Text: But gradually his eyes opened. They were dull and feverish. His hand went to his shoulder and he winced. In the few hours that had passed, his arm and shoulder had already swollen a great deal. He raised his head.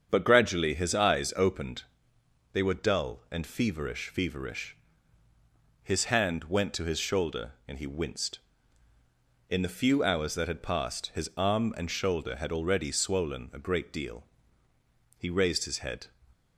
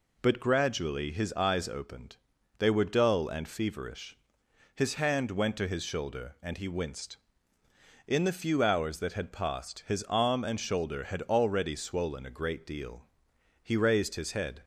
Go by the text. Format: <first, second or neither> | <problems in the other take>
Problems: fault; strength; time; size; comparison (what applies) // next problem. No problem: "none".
second | starts louder than the rest; strong; until 1.1 s; 7.5 dB // says "feverish" twice; at 4.1 s